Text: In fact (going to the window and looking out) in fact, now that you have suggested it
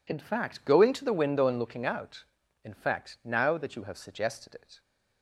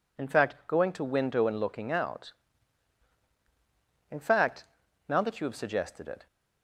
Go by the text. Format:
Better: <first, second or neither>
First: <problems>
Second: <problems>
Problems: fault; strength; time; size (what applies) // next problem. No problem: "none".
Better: first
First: none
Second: skips "the"; at 1.0 s